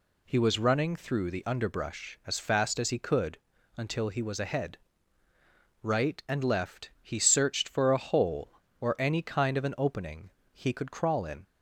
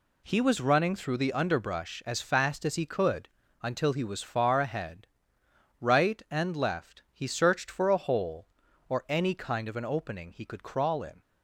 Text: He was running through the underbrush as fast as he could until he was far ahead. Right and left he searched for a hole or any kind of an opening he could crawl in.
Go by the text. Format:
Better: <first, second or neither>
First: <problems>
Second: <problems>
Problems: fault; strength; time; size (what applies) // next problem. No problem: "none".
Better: second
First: pauses between "could" and "until"; at 3.3 s; 0.38 s long // skips "far"; at 4.3 s // pauses between "opening" and "he"; slight; at 10.2 s; 0.24 s long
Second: pauses between "could" and "until"; slight; at 3.2 s; 0.32 s long